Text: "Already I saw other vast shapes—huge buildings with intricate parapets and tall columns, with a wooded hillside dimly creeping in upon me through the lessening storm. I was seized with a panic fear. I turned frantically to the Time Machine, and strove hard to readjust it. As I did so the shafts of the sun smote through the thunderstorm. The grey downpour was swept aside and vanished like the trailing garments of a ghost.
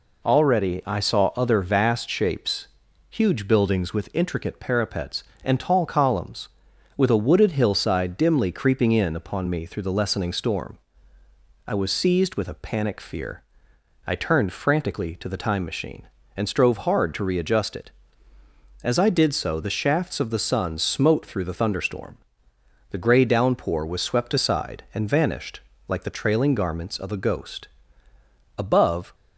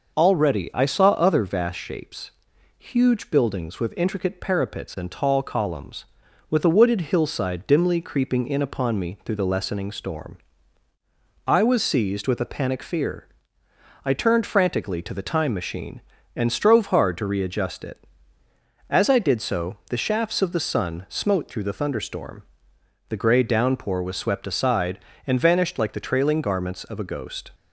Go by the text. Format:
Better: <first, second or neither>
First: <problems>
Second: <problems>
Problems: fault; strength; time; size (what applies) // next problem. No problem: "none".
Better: second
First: pauses between "vanished" and "like"; slight; at 25.6 s; 0.26 s long // goes on to say "Above"; from 28.5 s on; 0.58 s long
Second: none